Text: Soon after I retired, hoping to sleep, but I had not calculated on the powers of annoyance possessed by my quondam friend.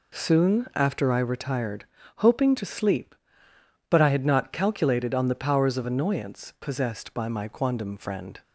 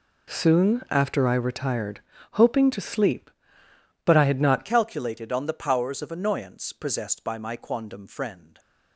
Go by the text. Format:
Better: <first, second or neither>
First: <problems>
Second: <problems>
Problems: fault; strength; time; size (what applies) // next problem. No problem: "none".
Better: first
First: none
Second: changes voice at "calculated"; from 4.6 s on; 3.9 s long